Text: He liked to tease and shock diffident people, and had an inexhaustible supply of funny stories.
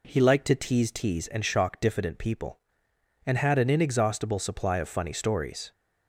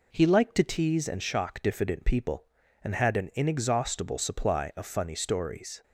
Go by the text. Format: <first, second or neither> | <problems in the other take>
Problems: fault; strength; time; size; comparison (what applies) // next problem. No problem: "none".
second | says "tease" twice; at 0.9 s